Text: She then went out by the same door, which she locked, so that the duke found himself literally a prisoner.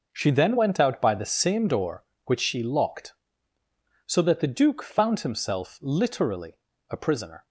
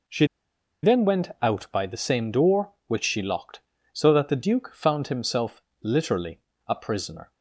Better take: first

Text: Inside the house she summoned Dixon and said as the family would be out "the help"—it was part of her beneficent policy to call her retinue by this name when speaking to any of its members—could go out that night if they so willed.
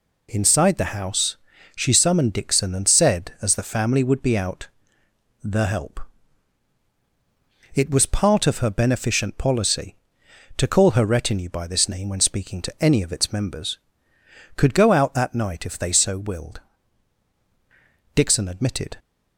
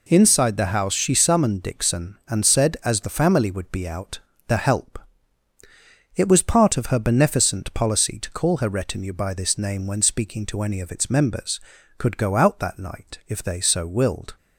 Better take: second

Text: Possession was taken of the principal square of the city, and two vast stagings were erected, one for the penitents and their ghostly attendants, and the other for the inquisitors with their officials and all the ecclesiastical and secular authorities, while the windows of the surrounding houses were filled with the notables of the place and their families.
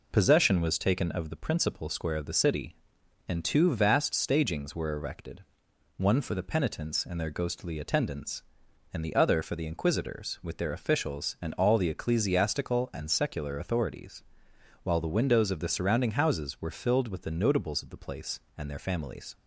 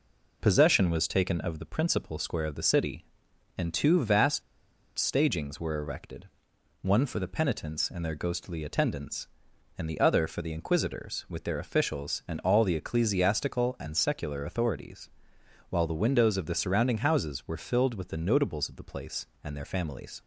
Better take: first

